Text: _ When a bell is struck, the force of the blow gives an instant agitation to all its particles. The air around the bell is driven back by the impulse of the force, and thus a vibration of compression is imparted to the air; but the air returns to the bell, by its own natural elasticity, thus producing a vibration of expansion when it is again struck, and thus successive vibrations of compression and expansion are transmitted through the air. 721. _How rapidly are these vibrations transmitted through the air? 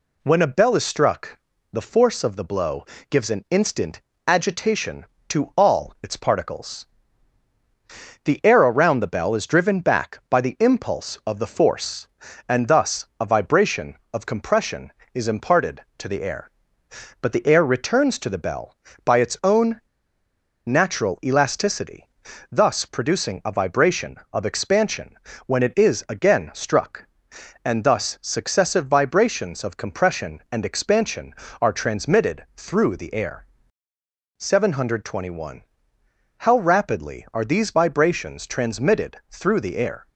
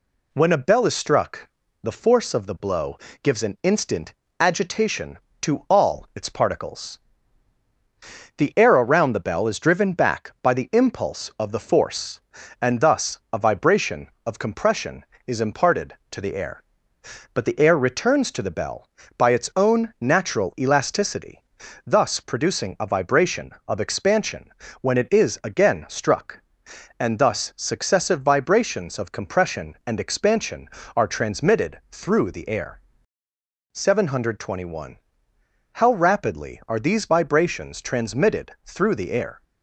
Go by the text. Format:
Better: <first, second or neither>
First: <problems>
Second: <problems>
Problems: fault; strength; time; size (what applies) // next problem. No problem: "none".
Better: second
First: pauses between "blow" and "gives"; slight; at 2.8 s; 0.24 s long // pauses between "instant" and "agitation"; slight; at 4.0 s; 0.24 s long // pauses between "own" and "natural"; noticeable; at 19.8 s; 0.86 s long // pauses between "expansion" and "when"; slight; at 25.1 s; 0.30 s long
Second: pauses between "blow" and "gives"; slight; at 2.9 s; 0.24 s long // pauses between "instant" and "agitation"; slight; at 4.1 s; 0.24 s long // pauses between "expansion" and "when"; slight; at 24.5 s; 0.30 s long